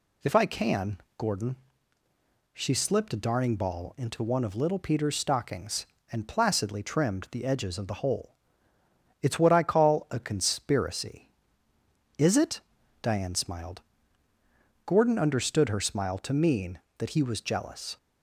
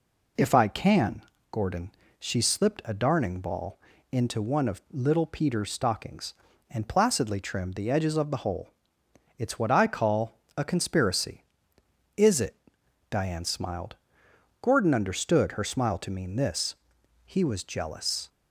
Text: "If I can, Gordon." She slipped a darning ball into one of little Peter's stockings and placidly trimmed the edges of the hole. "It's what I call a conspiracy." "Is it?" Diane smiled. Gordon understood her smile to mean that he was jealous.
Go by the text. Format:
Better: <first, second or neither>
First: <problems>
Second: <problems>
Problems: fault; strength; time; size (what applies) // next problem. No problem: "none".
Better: first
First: none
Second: pauses between "ball" and "into"; slight; at 3.7 s; 0.34 s long // pauses between "call" and "a"; slight; at 10.3 s; 0.18 s long // says "this" for "that"; at 16.3 s